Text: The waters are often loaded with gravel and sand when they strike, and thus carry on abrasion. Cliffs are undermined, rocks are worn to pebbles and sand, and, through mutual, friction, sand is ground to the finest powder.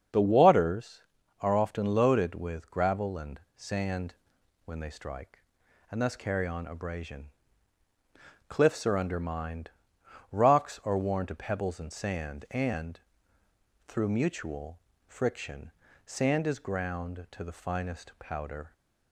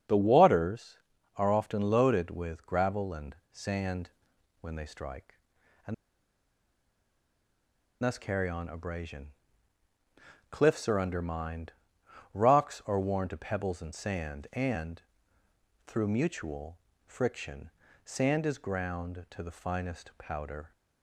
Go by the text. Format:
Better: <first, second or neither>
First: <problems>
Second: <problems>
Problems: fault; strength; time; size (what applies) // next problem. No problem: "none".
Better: first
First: starts louder than the rest; strong; until 1.5 s; 7 dB // pauses between "and" and "sand"; slight; at 3.4 s; 0.16 s long // pauses between "sand" and "when"; noticeable; at 4.1 s; 0.50 s long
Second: starts louder than the rest; strong; until 1.4 s; 7 dB // pauses between "and" and "sand"; slight; at 3.3 s; 0.16 s long // pauses between "sand" and "when"; noticeable; at 4.0 s; 0.50 s long // pauses between "and" and "thus"; strong; at 5.9 s; 2.0 s long